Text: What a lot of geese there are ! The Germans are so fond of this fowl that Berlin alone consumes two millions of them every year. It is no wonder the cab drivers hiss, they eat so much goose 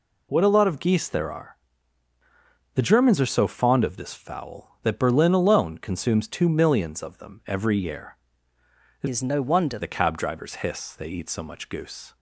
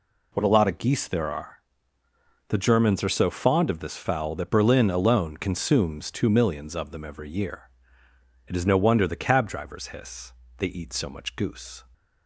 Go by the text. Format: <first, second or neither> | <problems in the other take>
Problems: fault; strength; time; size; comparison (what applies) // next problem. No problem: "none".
second | changes voice from "is" to "wonder"; from 9.0 to 9.7 s; 0.7 s long